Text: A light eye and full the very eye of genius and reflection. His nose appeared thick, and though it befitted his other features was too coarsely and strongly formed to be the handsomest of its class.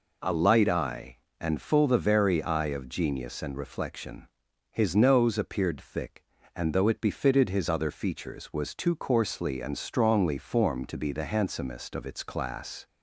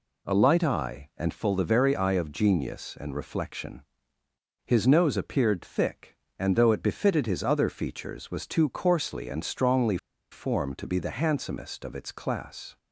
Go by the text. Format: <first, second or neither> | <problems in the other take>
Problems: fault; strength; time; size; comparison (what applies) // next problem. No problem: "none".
first | pauses between "strongly" and "formed"; slight; at 9.9 s; 0.34 s long